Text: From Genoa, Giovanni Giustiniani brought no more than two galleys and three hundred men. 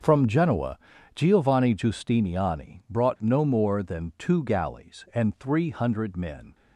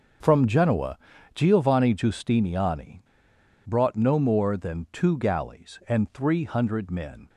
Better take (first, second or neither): first